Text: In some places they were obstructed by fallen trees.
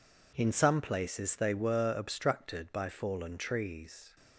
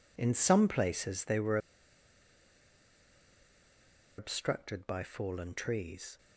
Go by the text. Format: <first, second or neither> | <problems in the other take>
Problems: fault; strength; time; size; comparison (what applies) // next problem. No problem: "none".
first | pauses between "were" and "obstructed"; strong; at 1.5 s; 2.6 s long